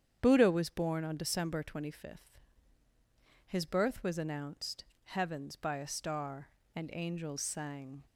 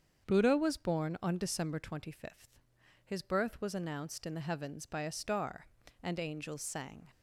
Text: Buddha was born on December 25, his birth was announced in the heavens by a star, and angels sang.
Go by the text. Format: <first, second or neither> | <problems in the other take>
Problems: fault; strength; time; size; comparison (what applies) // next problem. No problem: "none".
second | starts louder than the rest; strong; until 1.2 s; 8.5 dB; strong in the second // skips "in the"; at 4.9 s